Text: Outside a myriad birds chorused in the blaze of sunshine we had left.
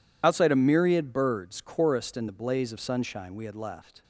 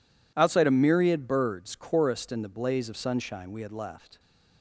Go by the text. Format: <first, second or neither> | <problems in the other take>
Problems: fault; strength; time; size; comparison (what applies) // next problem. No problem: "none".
second | loses the start of "Outside"; at 0.2 s; 45 ms